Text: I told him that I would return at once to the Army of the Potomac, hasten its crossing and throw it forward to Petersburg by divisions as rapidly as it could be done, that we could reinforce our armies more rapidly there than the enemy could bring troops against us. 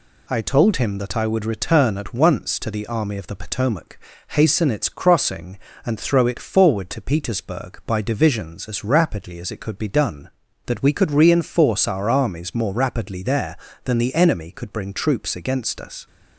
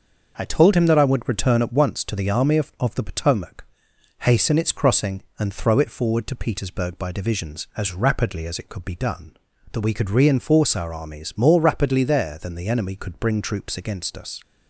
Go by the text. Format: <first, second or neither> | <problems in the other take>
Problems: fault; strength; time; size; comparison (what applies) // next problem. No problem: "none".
first | starts louder than the rest; noticeable; until 1.3 s; 6 dB // says "of" twice; at 2.7 s